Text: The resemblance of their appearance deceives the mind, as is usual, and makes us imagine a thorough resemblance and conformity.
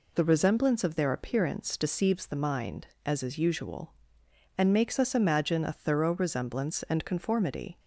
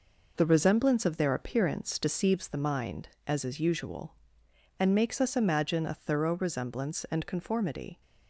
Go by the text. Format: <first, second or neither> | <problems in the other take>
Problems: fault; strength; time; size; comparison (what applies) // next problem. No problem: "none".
first | gets quieter; throughout; 6.5 dB